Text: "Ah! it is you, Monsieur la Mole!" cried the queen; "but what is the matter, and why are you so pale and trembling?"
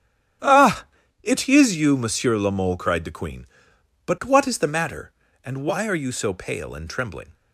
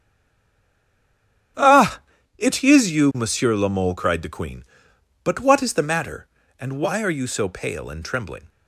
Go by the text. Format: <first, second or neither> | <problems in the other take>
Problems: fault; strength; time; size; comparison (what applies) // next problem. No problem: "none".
first | stays silent before the first word; noticeable; until 1.5 s; 1.5 s long // starts louder than the rest; strong; until 2.9 s; 10.5 dB; strong in the first